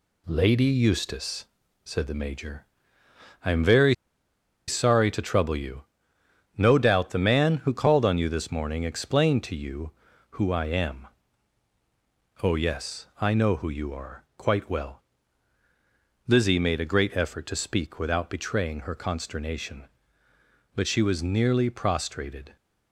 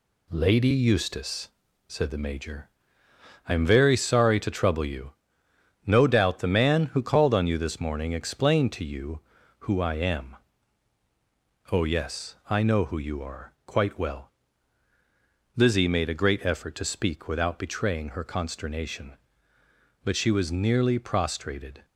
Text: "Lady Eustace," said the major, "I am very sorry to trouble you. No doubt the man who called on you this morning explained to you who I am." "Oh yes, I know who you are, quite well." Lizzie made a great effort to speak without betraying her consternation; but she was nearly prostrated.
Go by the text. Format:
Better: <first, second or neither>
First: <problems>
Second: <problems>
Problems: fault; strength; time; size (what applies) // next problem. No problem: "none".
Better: second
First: pauses between "very" and "sorry"; noticeable; at 3.9 s; 0.74 s long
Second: none